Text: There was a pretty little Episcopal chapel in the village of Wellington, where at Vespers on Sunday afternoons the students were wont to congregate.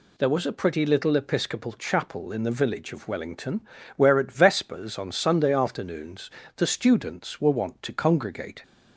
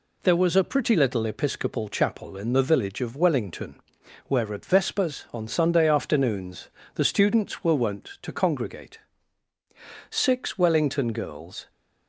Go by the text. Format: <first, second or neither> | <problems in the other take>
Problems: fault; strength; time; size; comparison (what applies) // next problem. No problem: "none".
first | pauses between "afternoons" and "the"; slight; at 6.6 s; 0.28 s long; slight in the first // goes on to say "Six Wellington girls"; from 10.0 s on; 1.6 s long